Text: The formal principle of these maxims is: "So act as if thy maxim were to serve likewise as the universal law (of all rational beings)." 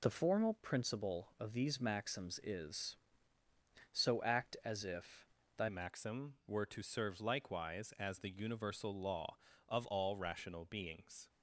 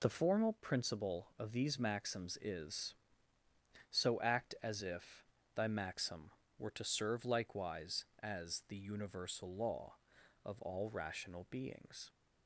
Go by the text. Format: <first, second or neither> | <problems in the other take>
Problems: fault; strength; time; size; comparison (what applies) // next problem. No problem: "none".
second | pauses between "if" and "thy"; slight; at 5.2 s; 0.26 s long; slight in the second // changes voice at "maxim"; from 5.6 s on; 5.6 s long